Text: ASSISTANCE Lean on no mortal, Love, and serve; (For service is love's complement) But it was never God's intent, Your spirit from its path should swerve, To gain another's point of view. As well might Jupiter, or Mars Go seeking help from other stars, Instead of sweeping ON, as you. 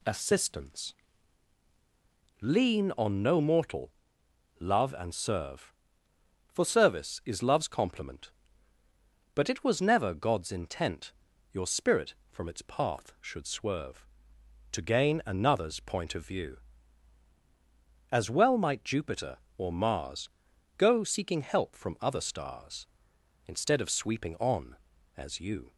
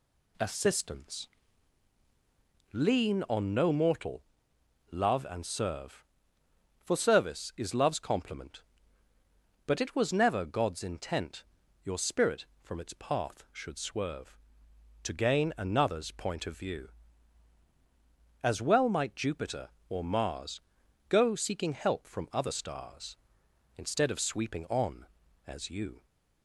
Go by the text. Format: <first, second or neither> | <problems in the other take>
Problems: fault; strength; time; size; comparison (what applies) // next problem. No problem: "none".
neither | pauses between "ASSISTANCE" and "Lean"; strong; the same in both // pauses between "Mars" and "Go"; noticeable; the same in both